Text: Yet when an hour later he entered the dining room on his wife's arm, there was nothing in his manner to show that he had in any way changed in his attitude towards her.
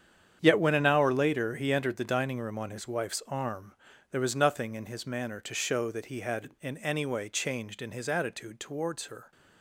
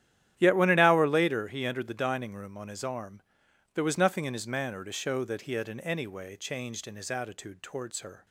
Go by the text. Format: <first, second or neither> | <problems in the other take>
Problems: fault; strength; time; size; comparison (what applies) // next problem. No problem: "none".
first | starts louder than the rest; strong; until 1.3 s; 11.5 dB; strong in the first // skips "wife's"; at 2.8 s